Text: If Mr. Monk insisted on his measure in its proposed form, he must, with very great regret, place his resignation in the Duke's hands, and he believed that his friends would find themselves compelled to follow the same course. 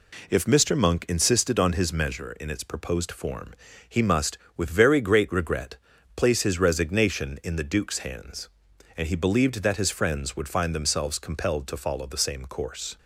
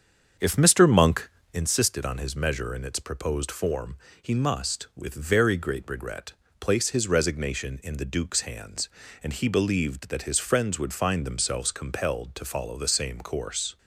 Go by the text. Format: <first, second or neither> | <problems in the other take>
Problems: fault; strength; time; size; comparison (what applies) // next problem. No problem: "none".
first | starts louder than the rest; strong; until 1.7 s; 7 dB // pauses between "Monk" and "insisted"; slight; at 1.2 s; 0.22 s long